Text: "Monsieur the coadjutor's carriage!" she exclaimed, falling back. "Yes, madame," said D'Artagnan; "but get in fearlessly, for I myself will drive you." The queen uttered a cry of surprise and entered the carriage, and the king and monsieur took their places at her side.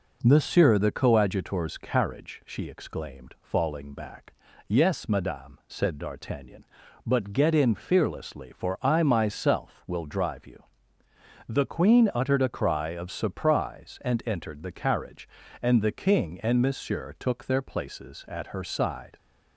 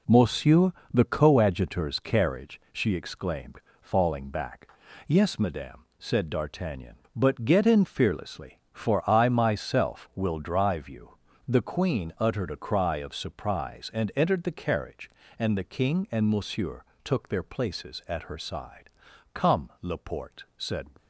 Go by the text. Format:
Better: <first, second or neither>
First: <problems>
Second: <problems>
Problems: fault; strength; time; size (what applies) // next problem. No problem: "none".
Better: first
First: none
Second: pauses between "Monsieur" and "the"; slight; at 0.7 s; 0.22 s long // pauses between "monsieur" and "took"; slight; at 16.8 s; 0.20 s long // goes on to say "Come Laporte said"; from 19.3 s on; 1.5 s long